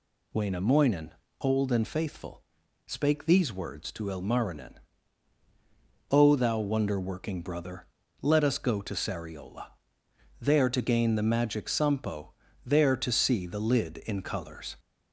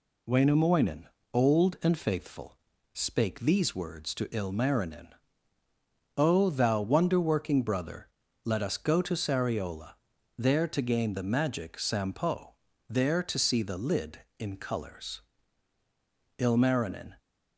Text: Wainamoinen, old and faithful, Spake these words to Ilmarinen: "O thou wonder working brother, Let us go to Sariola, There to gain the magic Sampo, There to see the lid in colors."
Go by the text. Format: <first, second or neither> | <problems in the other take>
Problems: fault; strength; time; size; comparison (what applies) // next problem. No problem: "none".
first | goes on to say "Ilmarinen"; noticeable; from 16.3 s on; 0.80 s long